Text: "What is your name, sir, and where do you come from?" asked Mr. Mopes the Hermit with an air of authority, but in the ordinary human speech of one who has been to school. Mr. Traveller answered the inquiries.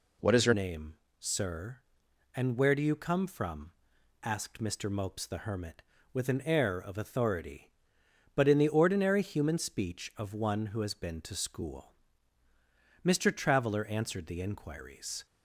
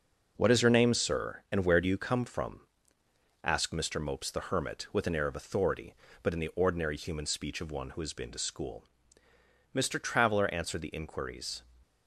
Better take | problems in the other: second | changes voice at "name"; from 0.5 s on; 14.7 s long

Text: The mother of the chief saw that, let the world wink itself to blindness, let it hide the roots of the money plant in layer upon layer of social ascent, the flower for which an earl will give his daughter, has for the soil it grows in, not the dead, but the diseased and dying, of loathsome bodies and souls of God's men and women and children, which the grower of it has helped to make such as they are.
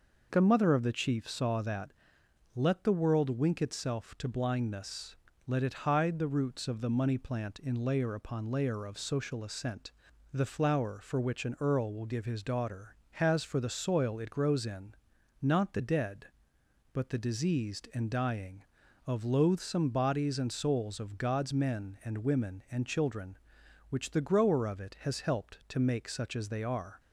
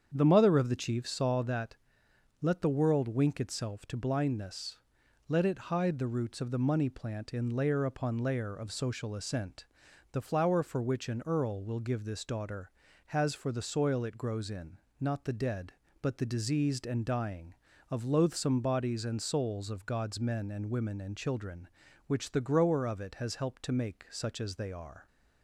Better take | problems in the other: first | starts louder than the rest; strong; until 1.1 s; 8 dB // says "this" for "his"; at 12.0 s

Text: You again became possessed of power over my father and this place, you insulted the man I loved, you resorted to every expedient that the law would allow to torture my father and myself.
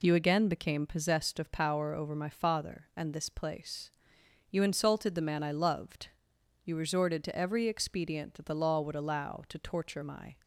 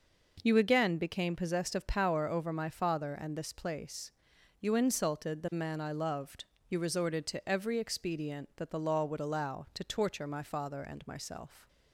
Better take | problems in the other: second | stops before "father and myself"; at 10.4 s

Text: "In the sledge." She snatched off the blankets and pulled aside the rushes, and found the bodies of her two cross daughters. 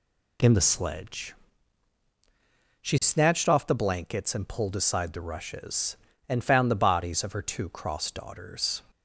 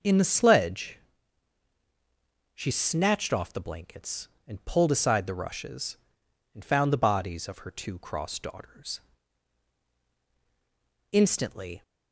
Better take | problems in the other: first | goes on to say "Instantly"; noticeable; from 11.1 s on; 0.70 s long

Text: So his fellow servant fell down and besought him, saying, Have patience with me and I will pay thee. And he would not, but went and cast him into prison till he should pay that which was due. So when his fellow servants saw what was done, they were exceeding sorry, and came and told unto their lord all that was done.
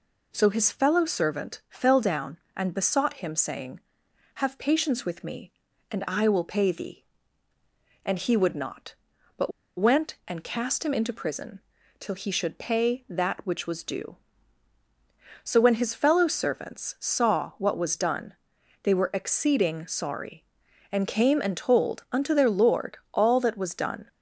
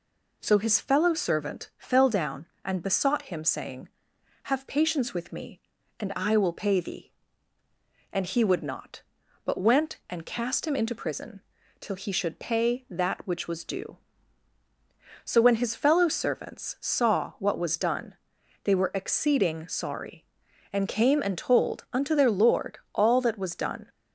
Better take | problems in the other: second | pauses between "but" and "went"; slight; at 9.5 s; 0.26 s long // pauses between "prison" and "till"; at 11.5 s; 0.40 s long; also in the second // pauses between "lord" and "all"; slight; at 22.9 s; 0.16 s long; slight in the second

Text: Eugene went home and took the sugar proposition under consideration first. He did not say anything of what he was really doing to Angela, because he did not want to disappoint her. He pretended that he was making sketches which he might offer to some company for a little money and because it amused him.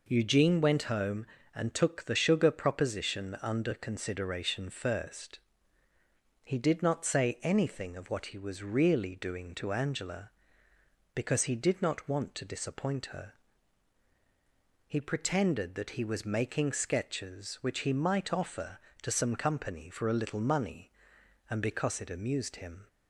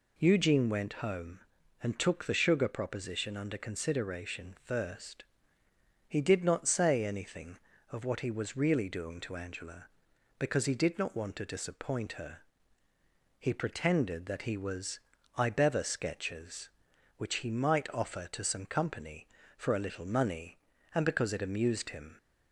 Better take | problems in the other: first | says "ibever" for "making"; at 15.3 s

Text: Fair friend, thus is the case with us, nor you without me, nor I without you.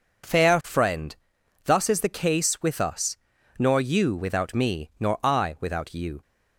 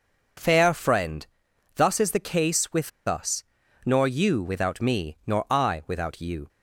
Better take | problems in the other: first | pauses between "with" and "us"; slight; at 2.9 s; 0.18 s long

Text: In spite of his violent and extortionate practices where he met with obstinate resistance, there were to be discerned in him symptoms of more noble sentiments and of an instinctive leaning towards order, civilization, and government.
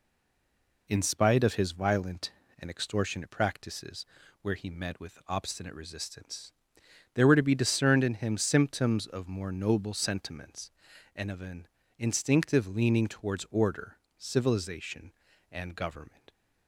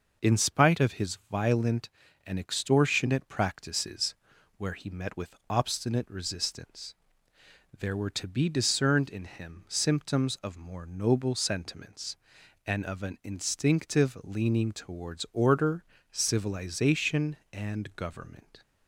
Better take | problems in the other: second | stays silent before the first word; slight; until 0.8 s; 0.8 s long // pauses between "practices" and "where"; slight; at 4.0 s; 0.36 s long; also in the second // pauses between "an" and "instinctive"; slight; at 11.6 s; 0.32 s long

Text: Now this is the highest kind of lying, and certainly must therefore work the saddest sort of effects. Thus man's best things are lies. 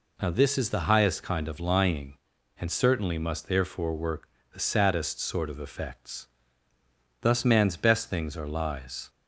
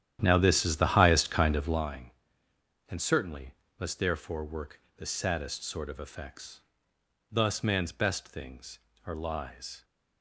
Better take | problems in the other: first | starts louder than the rest; strong; until 1.9 s; 10.5 dB // pauses between "certainly" and "must"; slight; at 3.5 s; 0.24 s long // pauses between "work" and "the"; slight; at 4.7 s; 0.20 s long; slight in the first

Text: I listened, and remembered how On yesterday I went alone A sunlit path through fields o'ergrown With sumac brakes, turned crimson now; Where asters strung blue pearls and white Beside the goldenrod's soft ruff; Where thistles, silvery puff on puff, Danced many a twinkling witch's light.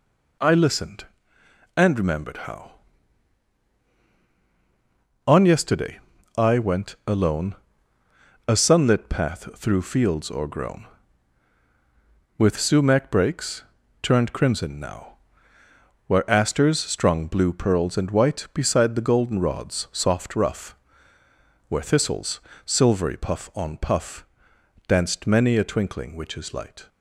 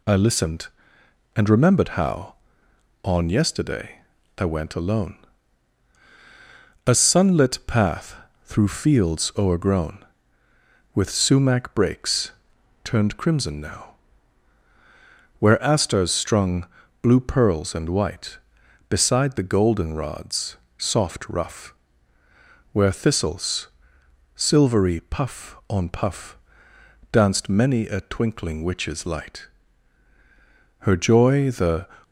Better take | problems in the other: first | pauses between "yesterday" and "I"; slight; at 4.0 s; 0.36 s long; slight in the first // pauses between "alone" and "A"; strong; at 5.1 s; 1.7 s long; noticeable in the first // pauses between "path" and "through"; slight; at 8.1 s; 0.26 s long // pauses between "strung" and "blue"; slight; at 16.6 s; 0.34 s long // pauses between "goldenrod's" and "soft"; slight; at 20.5 s; 0.22 s long // goes on to say "Her joy the"; noticeable; from 30.7 s on; 1.0 s long

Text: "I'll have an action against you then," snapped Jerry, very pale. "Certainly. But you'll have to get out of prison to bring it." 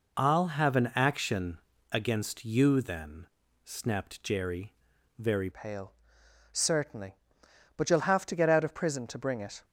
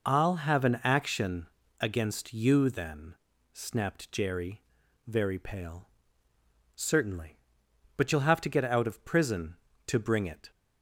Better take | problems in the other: second | pauses between "action" and "against"; slight; at 1.5 s; 0.34 s long; slight in the second // changes voice at "pale"; from 5.5 s on; 4.1 s long

